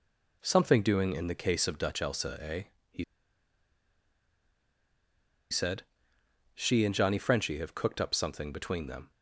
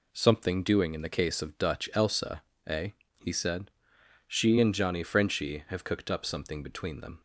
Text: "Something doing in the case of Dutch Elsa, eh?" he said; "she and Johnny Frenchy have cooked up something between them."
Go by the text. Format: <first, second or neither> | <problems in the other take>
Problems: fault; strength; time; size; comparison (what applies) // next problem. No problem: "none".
second | pauses between "he" and "said"; strong; at 3.0 s; 2.4 s long